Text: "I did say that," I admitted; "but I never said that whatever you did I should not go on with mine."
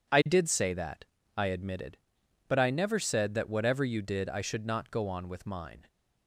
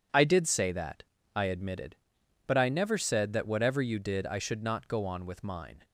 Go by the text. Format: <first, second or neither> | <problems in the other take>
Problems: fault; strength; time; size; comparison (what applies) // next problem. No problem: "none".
neither | none